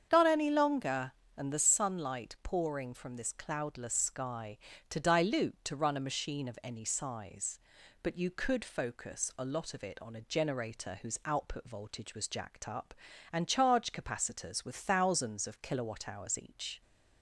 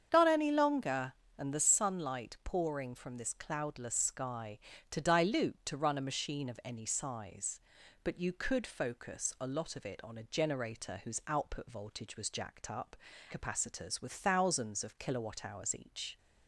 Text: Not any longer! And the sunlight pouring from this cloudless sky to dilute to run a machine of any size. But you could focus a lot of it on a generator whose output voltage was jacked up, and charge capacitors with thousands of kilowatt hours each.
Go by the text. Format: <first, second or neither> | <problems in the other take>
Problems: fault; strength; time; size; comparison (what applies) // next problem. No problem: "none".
first | starts louder than the rest; strong; until 1.1 s; 8 dB; strong in the first // skips "and charge"; at 13.1 s